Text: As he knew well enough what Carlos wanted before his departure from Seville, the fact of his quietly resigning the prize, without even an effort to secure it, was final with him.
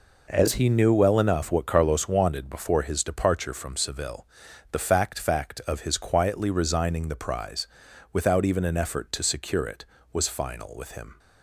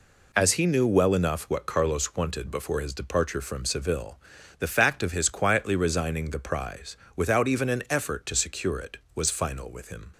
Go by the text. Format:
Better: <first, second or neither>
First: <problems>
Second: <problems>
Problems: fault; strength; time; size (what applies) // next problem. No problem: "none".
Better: second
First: says "fact" twice; at 5.1 s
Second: none